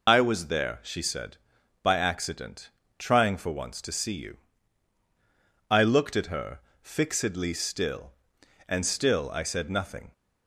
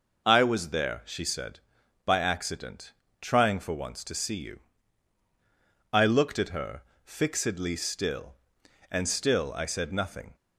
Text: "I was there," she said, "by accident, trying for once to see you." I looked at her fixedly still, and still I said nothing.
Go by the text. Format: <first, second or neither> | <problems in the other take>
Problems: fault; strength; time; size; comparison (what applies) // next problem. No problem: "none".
second | loses the start of "I"; at 0.0 s; 40 ms // pauses between "her" and "fixedly"; slight; at 6.6 s; 0.20 s long; slight in the second